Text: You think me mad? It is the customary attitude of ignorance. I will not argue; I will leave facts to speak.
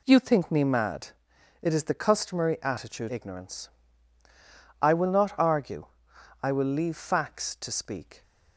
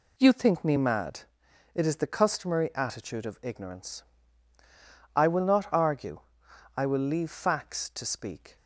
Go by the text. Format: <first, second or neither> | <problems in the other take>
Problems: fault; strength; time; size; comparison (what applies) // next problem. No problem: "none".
second | skips "of"; at 3.0 s